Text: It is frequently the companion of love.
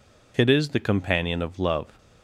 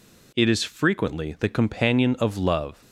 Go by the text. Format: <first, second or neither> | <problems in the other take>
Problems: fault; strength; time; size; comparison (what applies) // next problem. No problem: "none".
second | skips "frequently"; at 0.6 s